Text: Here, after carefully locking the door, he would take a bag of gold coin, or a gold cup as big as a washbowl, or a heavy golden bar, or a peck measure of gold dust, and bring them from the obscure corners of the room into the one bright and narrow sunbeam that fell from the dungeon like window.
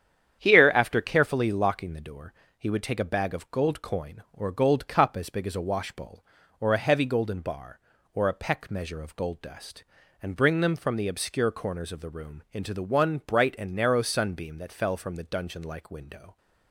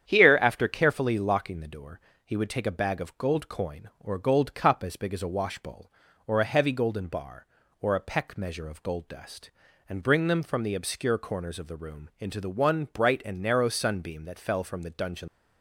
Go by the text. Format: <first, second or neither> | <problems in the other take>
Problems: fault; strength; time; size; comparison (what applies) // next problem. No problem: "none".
first | starts louder than the rest; strong; until 1.1 s; 9 dB; strong in the first // stops before "like window"; at 15.2 s